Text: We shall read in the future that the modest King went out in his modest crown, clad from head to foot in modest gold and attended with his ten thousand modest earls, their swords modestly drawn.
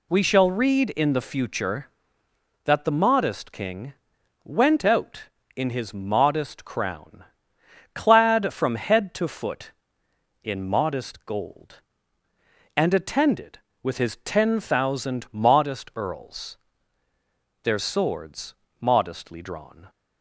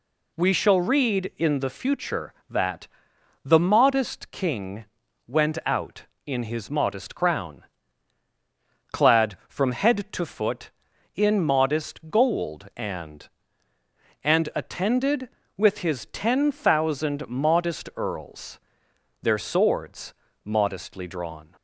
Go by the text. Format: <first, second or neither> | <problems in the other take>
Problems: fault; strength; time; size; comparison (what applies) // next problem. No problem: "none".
first | pauses between "that" and "the"; noticeable; at 2.8 s; 0.58 s long // pauses between "King" and "went"; at 4.8 s; 0.42 s long; noticeable in the first // says "and" twice; at 14.2 s // pauses between "swords" and "modestly"; slight; at 20.1 s; 0.30 s long; slight in the first